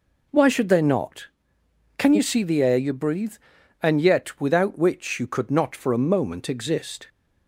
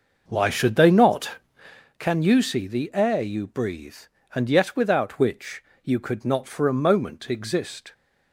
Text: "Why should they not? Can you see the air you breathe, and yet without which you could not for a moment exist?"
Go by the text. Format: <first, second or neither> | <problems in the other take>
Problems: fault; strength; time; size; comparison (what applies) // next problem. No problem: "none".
first | starts louder than the rest; noticeable; until 1.8 s; 6 dB // pauses between "which" and "you"; slight; at 5.6 s; 0.22 s long